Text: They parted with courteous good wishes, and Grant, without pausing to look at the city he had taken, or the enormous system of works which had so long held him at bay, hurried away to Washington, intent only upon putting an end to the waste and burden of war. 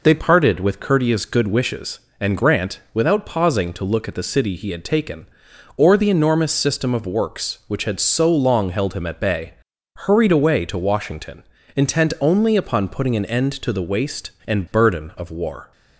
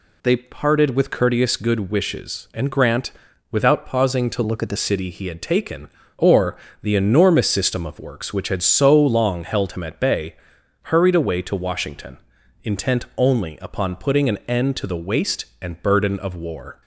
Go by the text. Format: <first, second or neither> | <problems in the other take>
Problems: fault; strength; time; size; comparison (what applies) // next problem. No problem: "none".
first | changes voice from "look" to "the"; from 4.4 to 4.7 s; 0.3 s long // pauses between "or" and "the"; slight; at 6.5 s; 0.26 s long